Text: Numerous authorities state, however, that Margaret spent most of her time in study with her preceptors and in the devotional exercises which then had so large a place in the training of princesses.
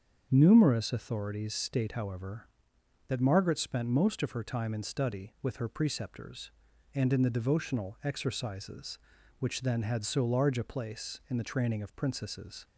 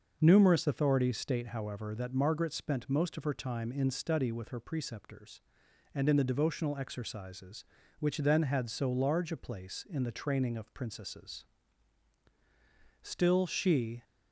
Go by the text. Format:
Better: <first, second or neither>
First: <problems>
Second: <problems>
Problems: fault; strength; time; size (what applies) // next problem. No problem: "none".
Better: first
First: starts louder than the rest; until 1.3 s; 7 dB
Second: starts louder than the rest; noticeable; until 1.2 s; 6 dB // goes on to say "Still she"; noticeable; from 13.0 s on; 1.0 s long